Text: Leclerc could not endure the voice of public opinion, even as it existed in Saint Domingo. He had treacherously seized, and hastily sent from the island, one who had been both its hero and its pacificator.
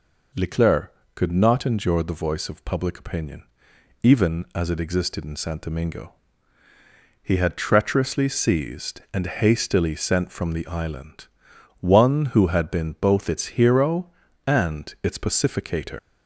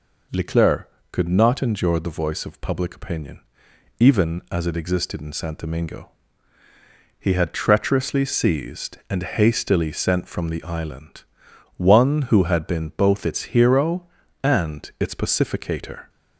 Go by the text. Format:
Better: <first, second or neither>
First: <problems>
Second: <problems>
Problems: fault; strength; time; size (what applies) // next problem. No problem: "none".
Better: second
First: leaves "pacificator" unfinished; at 15.9 s; 130 ms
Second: none